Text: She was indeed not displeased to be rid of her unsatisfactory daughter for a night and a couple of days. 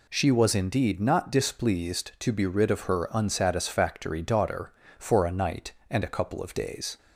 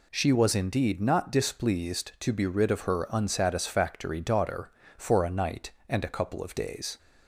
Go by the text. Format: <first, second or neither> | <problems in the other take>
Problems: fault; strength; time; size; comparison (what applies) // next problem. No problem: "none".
neither | none